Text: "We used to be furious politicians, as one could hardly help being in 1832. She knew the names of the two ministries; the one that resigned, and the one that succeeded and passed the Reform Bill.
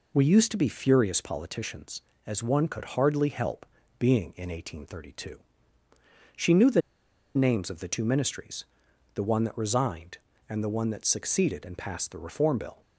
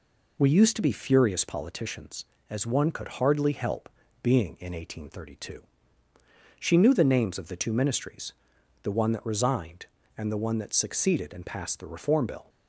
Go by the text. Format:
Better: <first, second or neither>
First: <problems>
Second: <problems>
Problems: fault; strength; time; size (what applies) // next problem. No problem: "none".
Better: second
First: pauses between "help" and "being"; slight; at 3.6 s; 0.32 s long // pauses between "the" and "names"; noticeable; at 6.8 s; 0.54 s long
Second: pauses between "help" and "being"; slight; at 3.8 s; 0.32 s long